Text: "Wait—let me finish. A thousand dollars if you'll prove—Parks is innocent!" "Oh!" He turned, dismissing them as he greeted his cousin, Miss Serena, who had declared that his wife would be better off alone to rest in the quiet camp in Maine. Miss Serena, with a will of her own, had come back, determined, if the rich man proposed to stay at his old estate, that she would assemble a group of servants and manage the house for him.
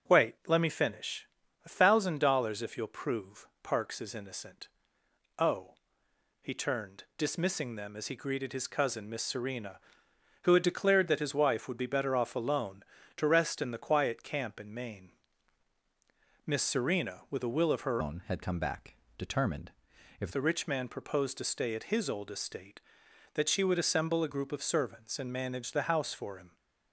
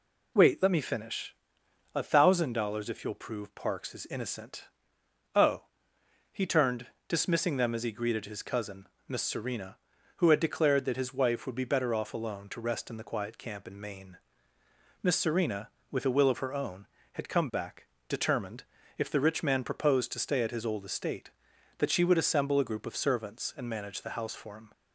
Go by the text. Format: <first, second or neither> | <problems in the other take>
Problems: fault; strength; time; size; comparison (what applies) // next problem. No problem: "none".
second | starts louder than the rest; until 1.1 s; 7 dB // changes voice from "own" to "if"; from 17.9 to 20.3 s; 2.4 s long